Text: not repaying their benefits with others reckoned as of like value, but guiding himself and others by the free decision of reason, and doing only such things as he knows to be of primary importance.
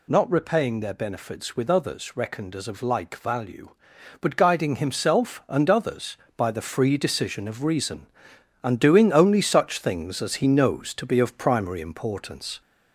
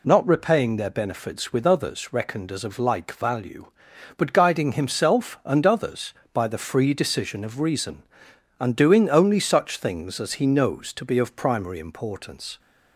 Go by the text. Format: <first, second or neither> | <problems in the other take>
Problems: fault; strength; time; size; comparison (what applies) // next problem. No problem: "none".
second | gets louder; slight; throughout; 2.5 dB